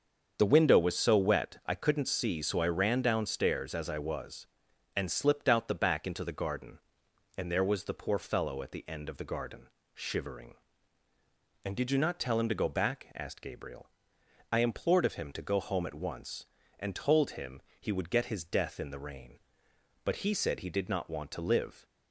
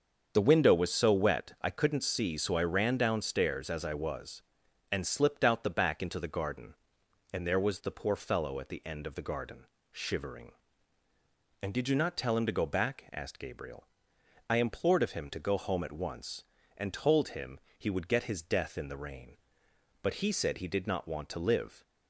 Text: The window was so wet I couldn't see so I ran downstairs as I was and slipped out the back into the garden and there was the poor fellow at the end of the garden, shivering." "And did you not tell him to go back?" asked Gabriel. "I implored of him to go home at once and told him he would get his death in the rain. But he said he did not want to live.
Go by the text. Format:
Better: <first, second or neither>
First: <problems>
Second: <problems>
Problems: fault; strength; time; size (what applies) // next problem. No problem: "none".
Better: neither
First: starts louder than the rest; until 1.4 s; 7 dB // pauses between "him" and "he"; slight; at 17.6 s; 0.18 s long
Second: starts louder than the rest; until 1.3 s; 7 dB // pauses between "him" and "he"; slight; at 17.5 s; 0.18 s long